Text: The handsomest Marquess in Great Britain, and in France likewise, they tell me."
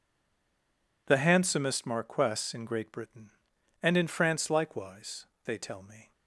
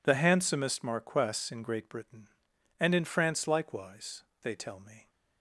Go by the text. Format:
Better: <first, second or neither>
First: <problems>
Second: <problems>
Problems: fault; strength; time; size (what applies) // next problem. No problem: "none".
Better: second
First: stays silent before the first word; until 1.0 s; 1.0 s long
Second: none